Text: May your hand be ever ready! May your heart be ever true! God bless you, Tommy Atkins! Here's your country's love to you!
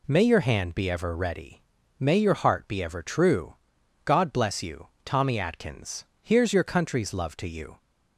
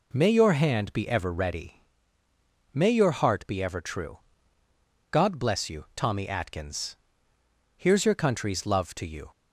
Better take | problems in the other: neither | none

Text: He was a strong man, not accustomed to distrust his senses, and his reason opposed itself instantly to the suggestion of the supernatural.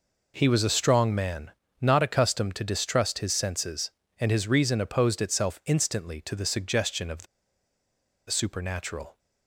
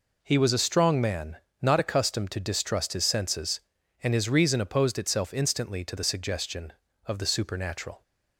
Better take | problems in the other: second | pauses between "the" and "supernatural"; at 7.2 s; 1.0 s long

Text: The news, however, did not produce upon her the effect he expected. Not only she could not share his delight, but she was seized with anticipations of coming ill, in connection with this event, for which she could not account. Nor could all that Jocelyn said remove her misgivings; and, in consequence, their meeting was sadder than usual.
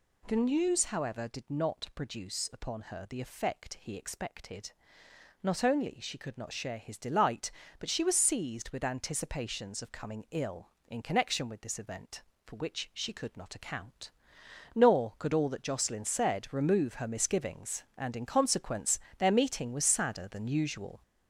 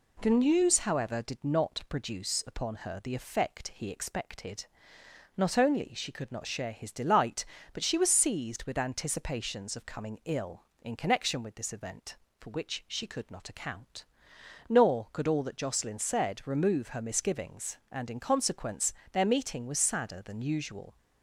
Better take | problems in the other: second | gets louder; noticeable; throughout; 4.5 dB

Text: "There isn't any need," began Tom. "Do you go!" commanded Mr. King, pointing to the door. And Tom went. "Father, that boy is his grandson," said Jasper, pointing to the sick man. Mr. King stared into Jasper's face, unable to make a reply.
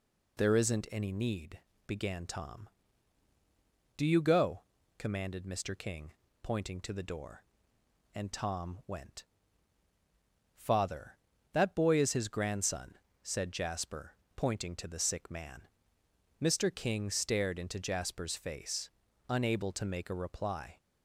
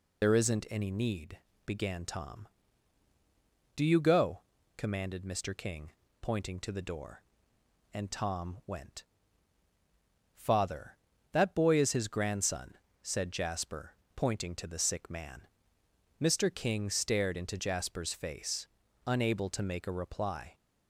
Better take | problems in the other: first | loses the start of "There"; at 0.2 s; 60 ms

